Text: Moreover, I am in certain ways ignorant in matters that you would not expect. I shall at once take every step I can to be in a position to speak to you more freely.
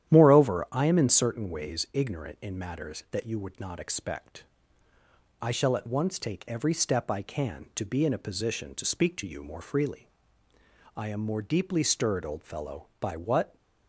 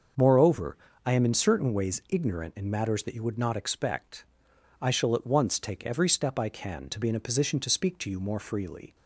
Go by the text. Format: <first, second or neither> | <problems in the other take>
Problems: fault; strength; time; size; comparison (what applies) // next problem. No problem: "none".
second | starts louder than the rest; strong; until 1.1 s; 11 dB; also in the second // goes on to say "I am more deeply stirred old fellow by what"; strong; from 10.9 s on; 2.6 s long